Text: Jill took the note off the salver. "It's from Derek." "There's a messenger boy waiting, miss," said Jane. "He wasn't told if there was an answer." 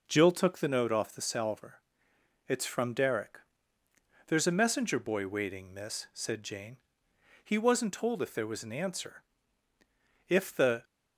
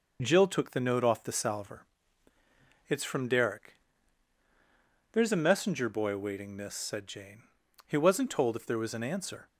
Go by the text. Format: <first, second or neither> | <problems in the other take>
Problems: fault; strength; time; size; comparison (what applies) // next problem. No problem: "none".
second | goes on to say "If the"; from 10.2 s on; 0.56 s long